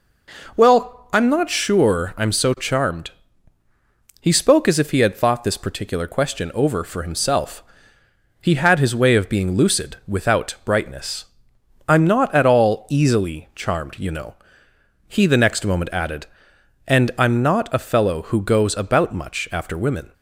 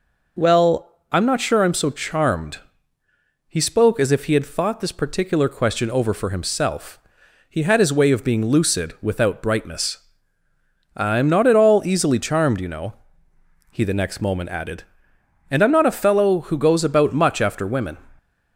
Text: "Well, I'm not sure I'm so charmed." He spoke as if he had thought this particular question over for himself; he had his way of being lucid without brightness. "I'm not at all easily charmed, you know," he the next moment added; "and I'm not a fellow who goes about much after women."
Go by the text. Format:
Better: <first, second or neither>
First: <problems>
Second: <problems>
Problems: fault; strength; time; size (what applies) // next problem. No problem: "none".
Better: neither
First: none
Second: none